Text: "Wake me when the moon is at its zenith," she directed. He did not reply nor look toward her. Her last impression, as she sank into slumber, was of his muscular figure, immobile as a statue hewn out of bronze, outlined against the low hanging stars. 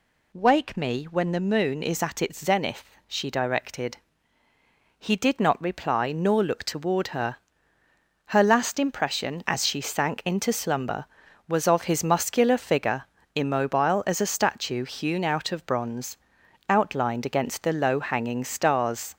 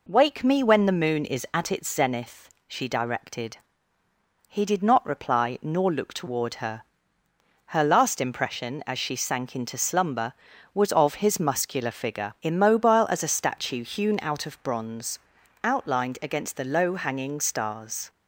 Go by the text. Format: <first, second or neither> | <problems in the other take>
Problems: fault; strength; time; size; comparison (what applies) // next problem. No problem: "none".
neither | none